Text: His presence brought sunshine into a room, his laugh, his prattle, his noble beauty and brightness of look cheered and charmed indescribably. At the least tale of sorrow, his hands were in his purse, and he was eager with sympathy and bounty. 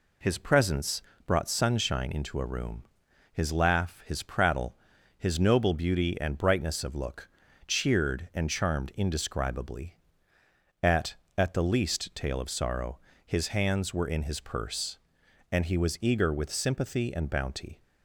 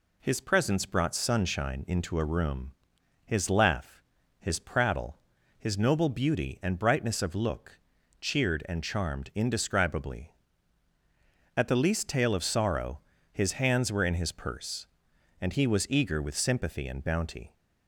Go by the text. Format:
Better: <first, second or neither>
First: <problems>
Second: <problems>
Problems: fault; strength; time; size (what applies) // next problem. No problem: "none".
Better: second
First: pauses between "presence" and "brought"; slight; at 1.0 s; 0.24 s long // pauses between "look" and "cheered"; at 7.2 s; 0.38 s long // says "At" twice; at 11.3 s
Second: pauses between "look" and "cheered"; at 7.7 s; 0.40 s long